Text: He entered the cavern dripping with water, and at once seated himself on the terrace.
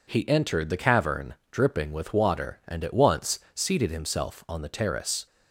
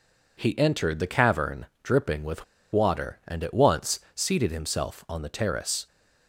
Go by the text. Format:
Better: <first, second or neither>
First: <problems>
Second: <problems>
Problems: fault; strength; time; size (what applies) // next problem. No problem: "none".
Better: first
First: pauses between "cavern" and "dripping"; slight; at 1.3 s; 0.16 s long // pauses between "once" and "seated"; slight; at 3.3 s; 0.16 s long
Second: pauses between "cavern" and "dripping"; slight; at 1.6 s; 0.16 s long // pauses between "with" and "water"; slight; at 2.4 s; 0.28 s long // pauses between "once" and "seated"; slight; at 4.0 s; 0.16 s long